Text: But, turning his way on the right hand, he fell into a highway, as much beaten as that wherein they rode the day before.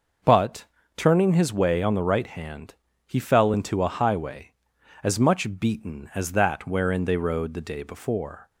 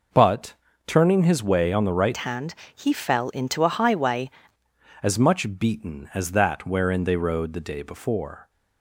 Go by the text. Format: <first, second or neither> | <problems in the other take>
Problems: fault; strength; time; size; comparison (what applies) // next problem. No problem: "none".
first | changes voice from "hand" to "highway"; from 2.1 to 4.2 s; 2.1 s long